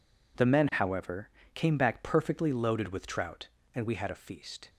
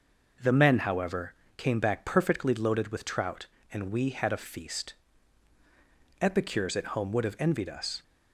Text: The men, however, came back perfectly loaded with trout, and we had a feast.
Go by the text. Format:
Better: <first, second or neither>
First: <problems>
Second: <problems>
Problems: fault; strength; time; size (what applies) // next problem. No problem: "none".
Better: first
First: none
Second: goes on to say "Epicures at home would have envied us"; strong; from 6.2 s on; 1.8 s long